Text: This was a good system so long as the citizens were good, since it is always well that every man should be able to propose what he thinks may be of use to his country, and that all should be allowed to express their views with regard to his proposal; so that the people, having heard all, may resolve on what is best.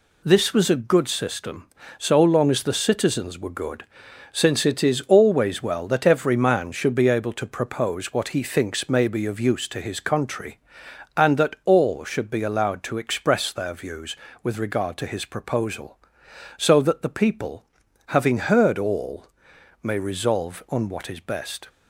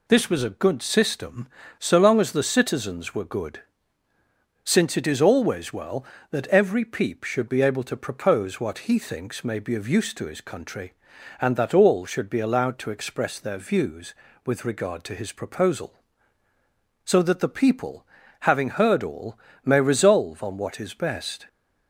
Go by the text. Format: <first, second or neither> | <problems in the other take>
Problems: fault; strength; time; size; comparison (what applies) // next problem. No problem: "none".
first | says "peep" for "man"; at 6.8 s